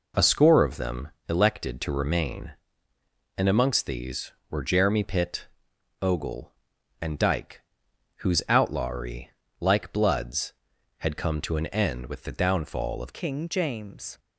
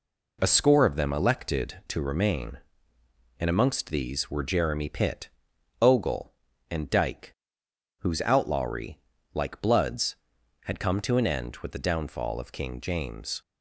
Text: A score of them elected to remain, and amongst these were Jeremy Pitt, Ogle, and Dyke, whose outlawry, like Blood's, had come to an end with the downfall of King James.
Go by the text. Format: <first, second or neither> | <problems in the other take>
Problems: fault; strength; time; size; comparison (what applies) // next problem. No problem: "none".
second | pauses between "them" and "elected"; slight; at 1.0 s; 0.18 s long // changes voice at "King"; from 13.1 s on; 1.0 s long